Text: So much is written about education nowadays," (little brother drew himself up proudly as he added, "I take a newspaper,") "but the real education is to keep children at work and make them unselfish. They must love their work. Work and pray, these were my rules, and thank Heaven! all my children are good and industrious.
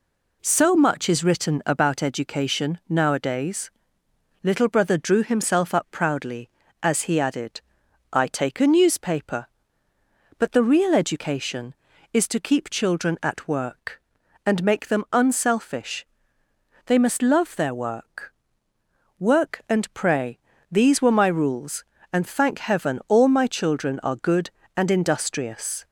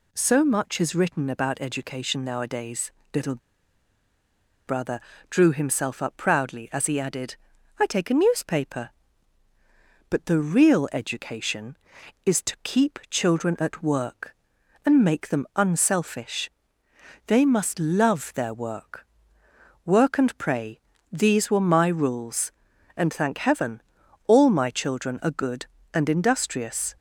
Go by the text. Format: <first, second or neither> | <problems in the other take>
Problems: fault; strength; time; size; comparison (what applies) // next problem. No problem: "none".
first | pauses between "little" and "brother"; strong; at 3.3 s; 1.3 s long // pauses between "brother" and "drew"; slight; at 4.9 s; 0.32 s long